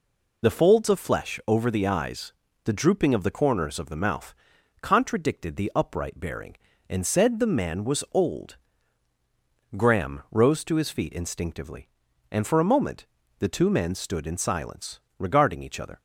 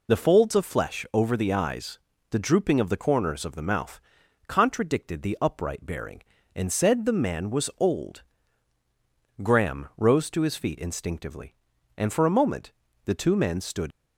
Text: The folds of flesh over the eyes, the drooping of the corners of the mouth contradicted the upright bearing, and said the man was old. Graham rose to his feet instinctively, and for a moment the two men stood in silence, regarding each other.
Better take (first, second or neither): first